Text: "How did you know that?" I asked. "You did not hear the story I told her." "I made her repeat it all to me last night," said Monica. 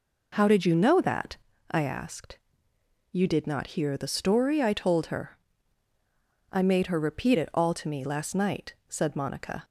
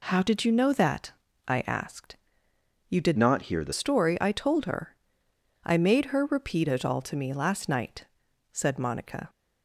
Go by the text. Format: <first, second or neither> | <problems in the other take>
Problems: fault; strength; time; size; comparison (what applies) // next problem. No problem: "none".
first | changes voice from "not" to "the"; from 3.1 to 3.7 s; 0.6 s long